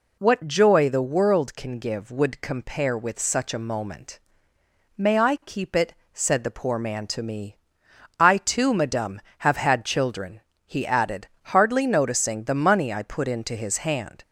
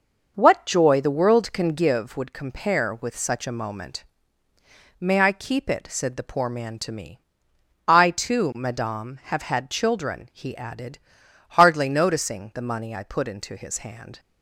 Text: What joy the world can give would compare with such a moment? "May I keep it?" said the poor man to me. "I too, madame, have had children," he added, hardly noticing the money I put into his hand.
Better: first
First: none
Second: starts louder than the rest; noticeable; until 2.0 s; 6 dB

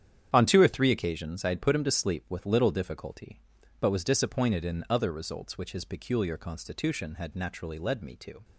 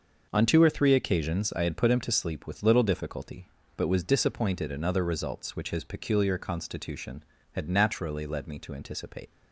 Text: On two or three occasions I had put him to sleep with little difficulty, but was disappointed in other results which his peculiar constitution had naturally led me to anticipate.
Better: second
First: starts louder than the rest; strong; until 1.3 s; 9.5 dB // stops before "anticipate"; at 8.4 s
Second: starts louder than the rest; noticeable; until 1.3 s; 6 dB

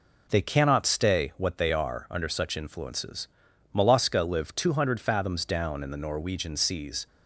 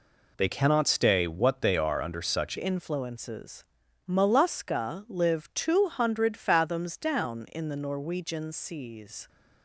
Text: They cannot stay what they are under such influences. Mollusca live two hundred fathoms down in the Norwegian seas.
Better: first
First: none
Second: changes voice at "influences"; from 2.5 s on; 6.7 s long

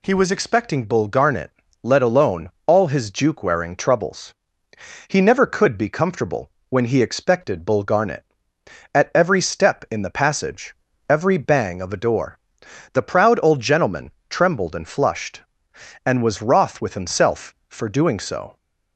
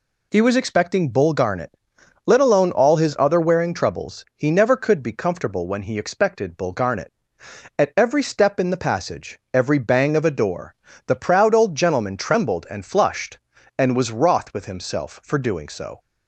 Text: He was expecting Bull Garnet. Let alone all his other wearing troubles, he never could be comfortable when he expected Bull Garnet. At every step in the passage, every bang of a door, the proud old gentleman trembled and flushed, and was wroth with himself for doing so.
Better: second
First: pauses between "alone" and "all"; slight; at 2.5 s; 0.16 s long // says "juke" for "other"; at 3.1 s // pauses between "comfortable" and "when"; slight; at 6.5 s; 0.20 s long // pauses between "gentleman" and "trembled"; slight; at 14.1 s; 0.18 s long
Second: none

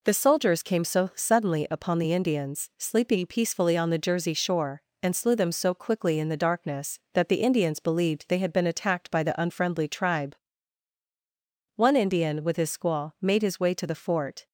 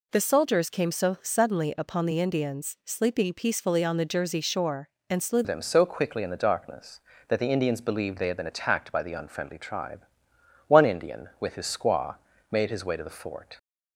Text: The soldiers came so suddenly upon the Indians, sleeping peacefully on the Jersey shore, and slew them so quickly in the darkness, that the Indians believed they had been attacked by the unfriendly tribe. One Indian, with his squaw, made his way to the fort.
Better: first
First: none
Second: changes voice at "them"; from 5.4 s on; 8.1 s long

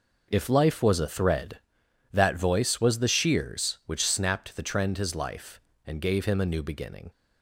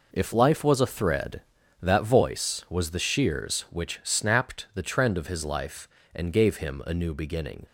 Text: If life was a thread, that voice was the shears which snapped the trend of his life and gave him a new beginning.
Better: second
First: skips "of"; at 4.9 s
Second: none

